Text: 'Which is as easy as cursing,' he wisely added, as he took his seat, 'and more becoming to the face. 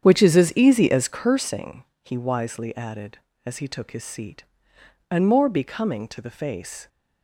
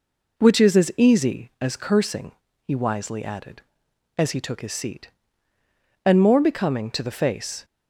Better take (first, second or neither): second